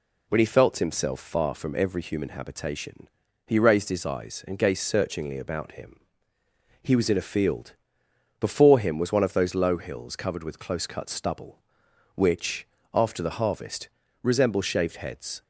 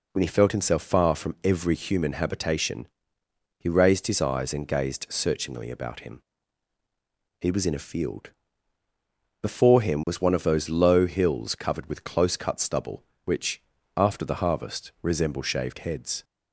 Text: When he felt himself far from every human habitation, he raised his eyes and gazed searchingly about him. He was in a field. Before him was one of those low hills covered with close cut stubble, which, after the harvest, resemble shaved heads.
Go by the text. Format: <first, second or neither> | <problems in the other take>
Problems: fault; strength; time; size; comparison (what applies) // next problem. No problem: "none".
neither | none